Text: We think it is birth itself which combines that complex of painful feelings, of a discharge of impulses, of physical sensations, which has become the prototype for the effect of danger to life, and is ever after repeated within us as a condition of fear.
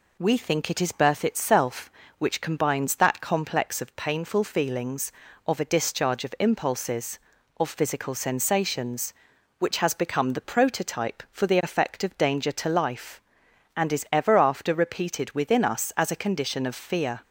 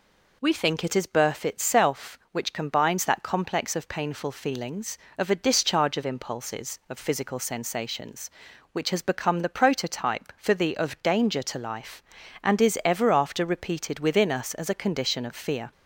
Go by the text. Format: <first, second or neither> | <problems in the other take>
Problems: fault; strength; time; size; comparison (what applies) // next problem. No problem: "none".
first | skips "effect"; at 10.7 s